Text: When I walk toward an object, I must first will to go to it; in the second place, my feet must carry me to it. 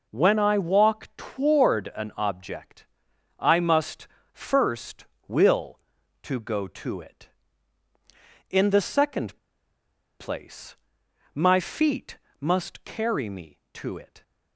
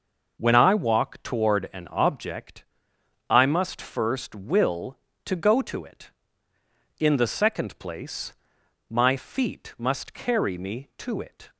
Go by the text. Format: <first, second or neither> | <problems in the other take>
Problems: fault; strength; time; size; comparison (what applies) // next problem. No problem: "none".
second | pauses between "must" and "first"; slight; at 4.0 s; 0.24 s long // pauses between "second" and "place"; noticeable; at 9.3 s; 0.83 s long // pauses between "feet" and "must"; slight; at 12.1 s; 0.24 s long